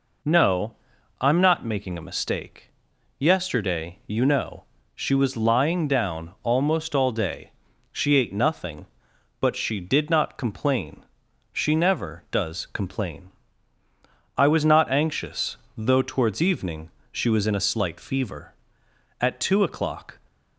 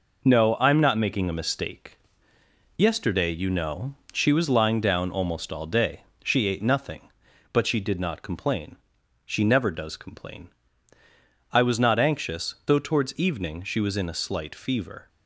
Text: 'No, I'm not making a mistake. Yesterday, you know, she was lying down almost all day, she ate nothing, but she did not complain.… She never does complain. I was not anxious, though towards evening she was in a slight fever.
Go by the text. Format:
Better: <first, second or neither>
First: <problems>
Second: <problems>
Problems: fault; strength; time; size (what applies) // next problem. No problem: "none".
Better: second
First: pauses between "evening" and "she"; slight; at 16.8 s; 0.22 s long // goes on to say "At two o'clock"; noticeable; from 19.2 s on; 0.98 s long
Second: none